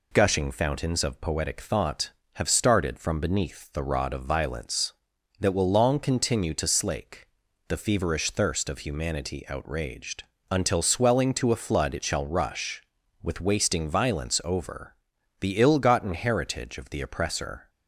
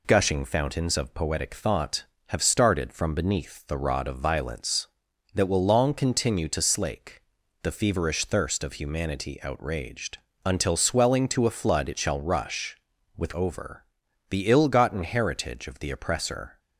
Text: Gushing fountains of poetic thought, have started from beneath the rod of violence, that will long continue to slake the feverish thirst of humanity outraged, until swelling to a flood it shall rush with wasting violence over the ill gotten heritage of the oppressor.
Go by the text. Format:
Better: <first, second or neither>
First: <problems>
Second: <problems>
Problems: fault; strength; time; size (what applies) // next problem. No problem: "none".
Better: first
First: pauses between "slake" and "the"; at 7.2 s; 0.42 s long // pauses between "over" and "the"; at 14.9 s; 0.44 s long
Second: pauses between "slake" and "the"; at 7.2 s; 0.42 s long // skips "wasting violence"; at 13.3 s // pauses between "over" and "the"; at 13.8 s; 0.44 s long